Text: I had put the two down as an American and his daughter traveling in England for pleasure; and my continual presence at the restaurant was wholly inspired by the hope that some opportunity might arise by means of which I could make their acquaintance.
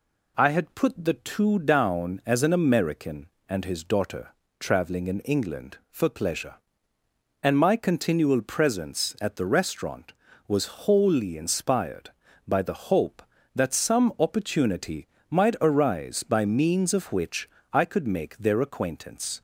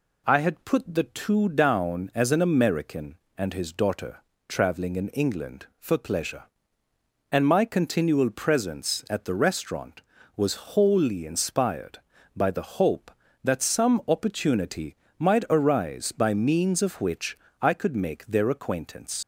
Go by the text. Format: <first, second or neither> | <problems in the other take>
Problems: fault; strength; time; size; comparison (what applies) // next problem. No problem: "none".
first | pauses between "daughter" and "traveling"; slight; at 4.2 s; 0.26 s long; slight in the first // pauses between "opportunity" and "might"; slight; at 14.9 s; 0.22 s long; slight in the first // pauses between "which" and "I"; slight; at 17.3 s; 0.22 s long; slight in the first // leaves "acquaintance" unfinished; at 19.2 s; 70 ms